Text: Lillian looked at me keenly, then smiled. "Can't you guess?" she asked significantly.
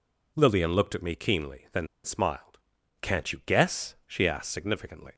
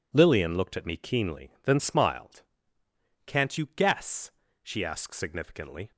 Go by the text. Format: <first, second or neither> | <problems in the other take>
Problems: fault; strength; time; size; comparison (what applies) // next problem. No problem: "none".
second | pauses between "then" and "smiled"; slight; at 1.8 s; 0.17 s long